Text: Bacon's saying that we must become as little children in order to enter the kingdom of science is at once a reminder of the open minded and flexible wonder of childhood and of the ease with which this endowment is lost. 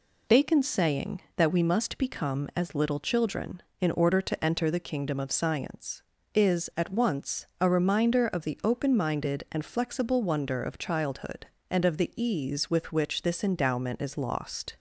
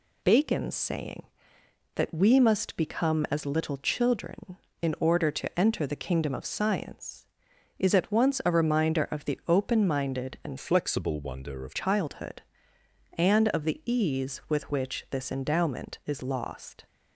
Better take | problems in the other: first | changes voice from "flexible" to "of"; from 10.5 to 11.7 s; 1.2 s long

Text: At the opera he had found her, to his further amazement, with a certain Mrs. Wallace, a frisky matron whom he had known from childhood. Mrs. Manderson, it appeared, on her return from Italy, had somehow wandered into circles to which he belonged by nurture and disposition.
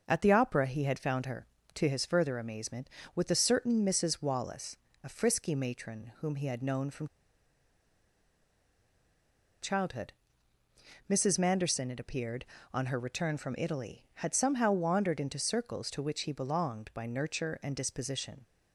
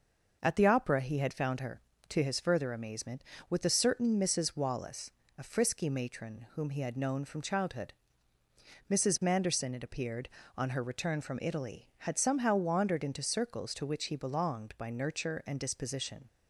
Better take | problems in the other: second | pauses between "from" and "childhood"; strong; at 7.0 s; 2.5 s long

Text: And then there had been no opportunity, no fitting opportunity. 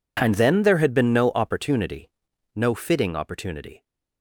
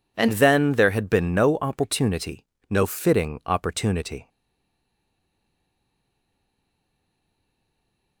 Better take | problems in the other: first | stays silent after the last word; strong; from 4.2 s on; 4.0 s long

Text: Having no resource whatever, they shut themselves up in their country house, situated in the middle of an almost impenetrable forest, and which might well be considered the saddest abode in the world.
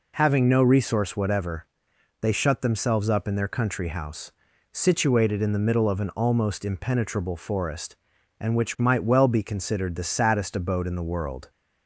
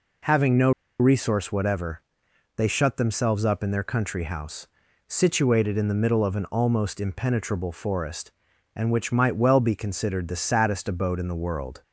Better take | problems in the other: first | pauses between "no" and "resource"; slight; at 0.7 s; 0.28 s long

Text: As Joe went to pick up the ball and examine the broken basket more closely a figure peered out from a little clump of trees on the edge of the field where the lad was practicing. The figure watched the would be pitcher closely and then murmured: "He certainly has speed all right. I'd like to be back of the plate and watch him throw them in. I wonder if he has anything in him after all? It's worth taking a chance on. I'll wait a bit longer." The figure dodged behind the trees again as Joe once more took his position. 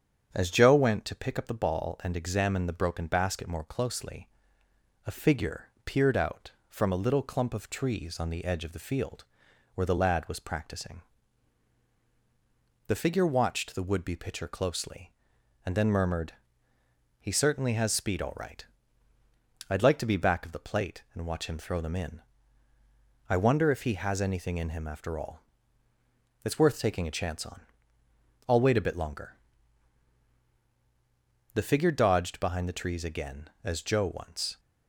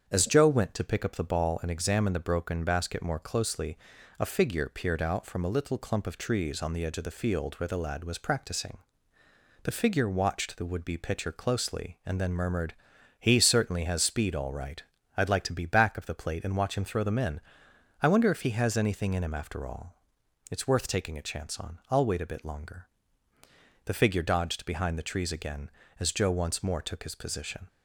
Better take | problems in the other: second | starts louder than the rest; strong; until 1.3 s; 8 dB; strong in the second // pauses between "closely" and "a"; noticeable; at 4.2 s; 0.78 s long; also in the second // pauses between "figure" and "peered"; slight; at 5.6 s; 0.18 s long // pauses between "field" and "where"; noticeable; at 9.2 s; 0.48 s long // stops before "more took his position"; at 34.5 s

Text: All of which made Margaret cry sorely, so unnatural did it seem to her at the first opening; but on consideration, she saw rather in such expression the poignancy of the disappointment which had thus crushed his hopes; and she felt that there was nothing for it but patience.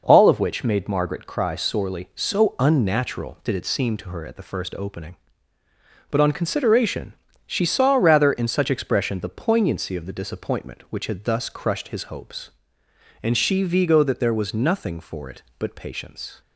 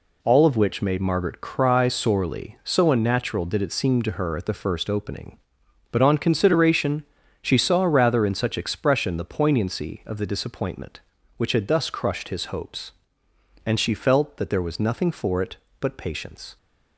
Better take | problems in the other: second | says "vigo" for "felt"; at 13.6 s

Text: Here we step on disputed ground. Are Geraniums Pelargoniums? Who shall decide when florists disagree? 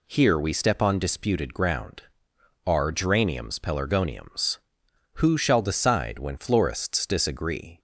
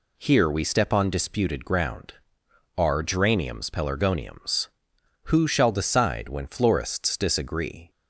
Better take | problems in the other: neither | none

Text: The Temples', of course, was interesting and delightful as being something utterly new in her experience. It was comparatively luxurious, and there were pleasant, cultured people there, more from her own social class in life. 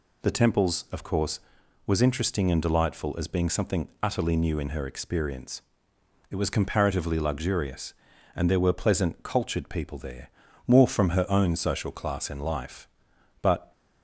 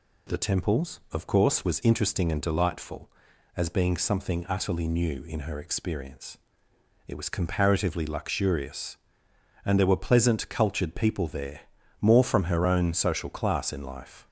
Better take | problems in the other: second | goes on to say "But"; slight; from 13.4 s on; 0.30 s long

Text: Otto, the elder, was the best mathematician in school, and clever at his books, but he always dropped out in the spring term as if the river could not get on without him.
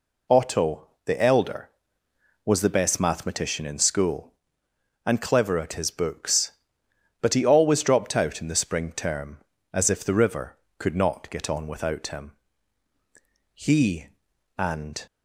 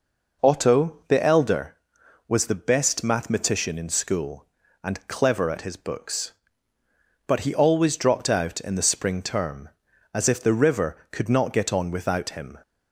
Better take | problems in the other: second | goes on to say "He and"; from 13.5 s on; 1.5 s long

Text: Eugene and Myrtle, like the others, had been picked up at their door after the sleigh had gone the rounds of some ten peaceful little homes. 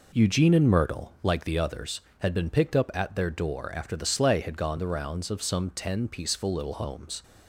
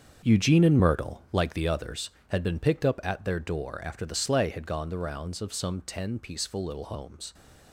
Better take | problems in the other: first | gets quieter; strong; throughout; 10.5 dB

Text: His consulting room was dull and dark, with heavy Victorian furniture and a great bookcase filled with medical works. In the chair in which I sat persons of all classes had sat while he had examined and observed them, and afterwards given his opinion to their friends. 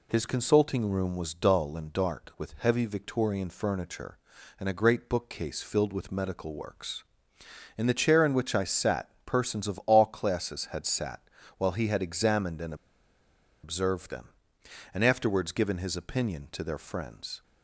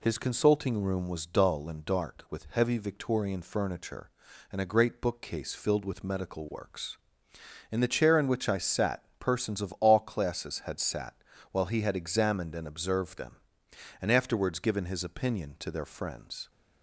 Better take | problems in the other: second | pauses between "sat" and "while"; at 11.1 s; 0.38 s long; also in the second // pauses between "and" and "observed"; noticeable; at 12.7 s; 0.89 s long

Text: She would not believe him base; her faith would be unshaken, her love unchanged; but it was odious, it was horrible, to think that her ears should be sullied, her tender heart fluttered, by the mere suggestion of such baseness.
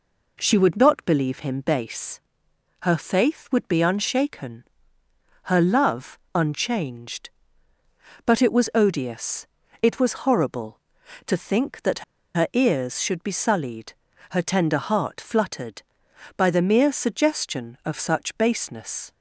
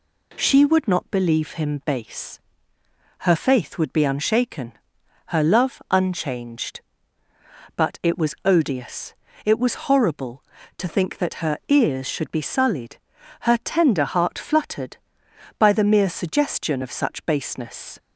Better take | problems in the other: second | pauses between "love" and "unchanged"; slight; at 6.1 s; 0.16 s long // pauses between "that" and "her"; slight; at 12.0 s; 0.33 s long

